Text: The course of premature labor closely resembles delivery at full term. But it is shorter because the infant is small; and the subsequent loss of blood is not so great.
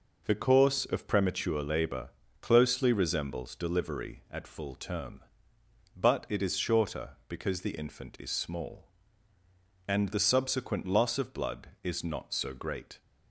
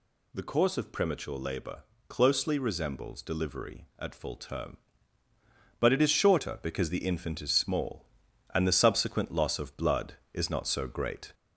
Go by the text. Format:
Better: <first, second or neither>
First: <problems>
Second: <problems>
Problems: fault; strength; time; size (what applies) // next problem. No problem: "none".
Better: first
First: pauses between "labor" and "closely"; slight; at 2.0 s; 0.32 s long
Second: gets louder; slight; throughout; 2 dB // pauses between "labor" and "closely"; slight; at 1.8 s; 0.24 s long